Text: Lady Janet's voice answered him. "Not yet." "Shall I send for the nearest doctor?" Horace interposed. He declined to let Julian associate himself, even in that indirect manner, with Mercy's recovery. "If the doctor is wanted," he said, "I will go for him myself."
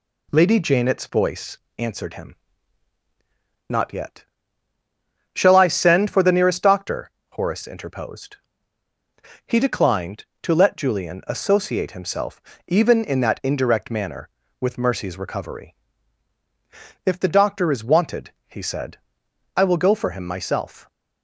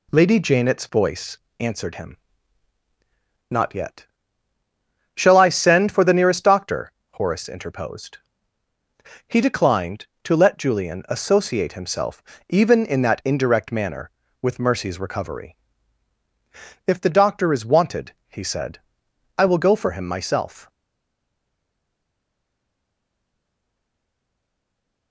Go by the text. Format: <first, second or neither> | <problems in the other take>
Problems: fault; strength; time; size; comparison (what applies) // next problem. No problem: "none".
first | pauses between "voice" and "answered"; slight; at 1.3 s; 0.22 s long; slight in the first // stays silent after the last word; strong; from 20.7 s on; 4.4 s long